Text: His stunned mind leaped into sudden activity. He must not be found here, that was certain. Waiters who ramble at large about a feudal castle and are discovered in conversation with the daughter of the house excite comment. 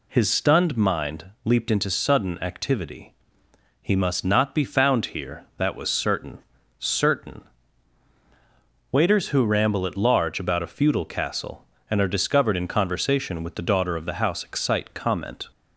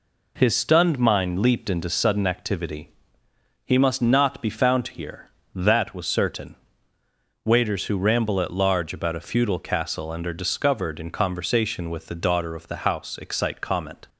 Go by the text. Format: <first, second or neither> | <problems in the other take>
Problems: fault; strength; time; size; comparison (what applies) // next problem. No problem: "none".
second | pauses between "mind" and "leaped"; slight; at 1.2 s; 0.18 s long // says "certain" twice; at 6.8 s